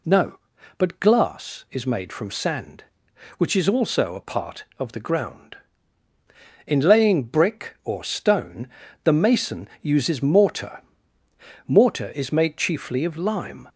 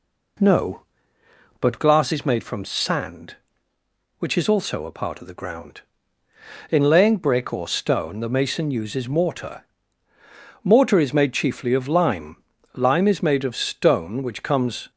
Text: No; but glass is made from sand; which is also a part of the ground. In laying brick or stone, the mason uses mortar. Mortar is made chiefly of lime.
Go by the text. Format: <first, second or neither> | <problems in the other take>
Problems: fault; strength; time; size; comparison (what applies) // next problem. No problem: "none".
first | goes on to say "Lime is made of stone which comes"; strong; from 12.7 s on; 2.1 s long